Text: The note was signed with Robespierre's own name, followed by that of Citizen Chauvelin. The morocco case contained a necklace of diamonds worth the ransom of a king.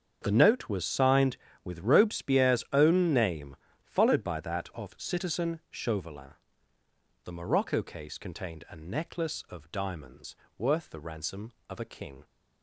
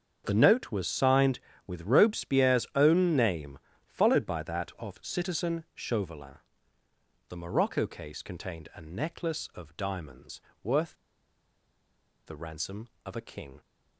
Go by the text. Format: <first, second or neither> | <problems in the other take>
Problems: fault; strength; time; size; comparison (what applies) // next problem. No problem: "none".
first | starts louder than the rest; strong; until 1.2 s; 7 dB; strong in the first // pauses between "diamonds" and "worth"; slight; at 10.4 s; 0.22 s long; slight in the first // pauses between "worth" and "the"; strong; at 10.9 s; 1.3 s long